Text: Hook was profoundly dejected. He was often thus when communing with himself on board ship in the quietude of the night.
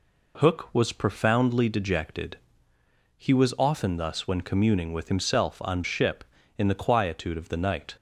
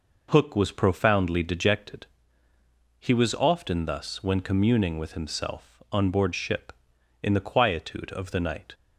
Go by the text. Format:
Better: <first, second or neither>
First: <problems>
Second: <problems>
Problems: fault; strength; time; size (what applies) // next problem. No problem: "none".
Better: second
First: skips "board"; at 5.8 s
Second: none